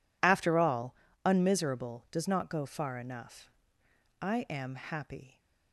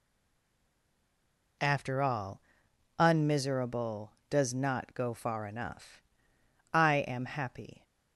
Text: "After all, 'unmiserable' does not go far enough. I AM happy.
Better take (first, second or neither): first